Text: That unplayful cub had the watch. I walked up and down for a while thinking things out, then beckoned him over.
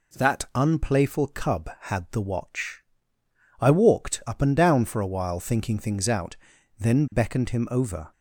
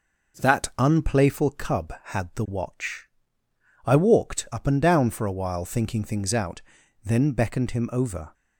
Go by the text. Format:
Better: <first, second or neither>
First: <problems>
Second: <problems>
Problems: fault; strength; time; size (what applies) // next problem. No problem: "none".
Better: first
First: none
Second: starts louder than the rest; noticeable; until 1.6 s; 5.5 dB